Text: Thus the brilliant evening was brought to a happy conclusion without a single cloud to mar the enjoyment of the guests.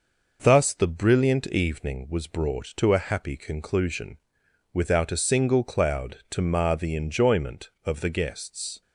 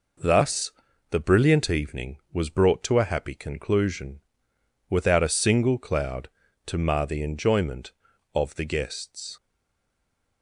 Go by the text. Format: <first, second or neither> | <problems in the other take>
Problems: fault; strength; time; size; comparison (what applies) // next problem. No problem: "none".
first | pauses between "Thus" and "the"; at 0.7 s; 0.38 s long // pauses between "conclusion" and "without"; noticeable; at 4.2 s; 0.70 s long; noticeable in the first // stays silent after the last word; from 9.3 s on; 1.1 s long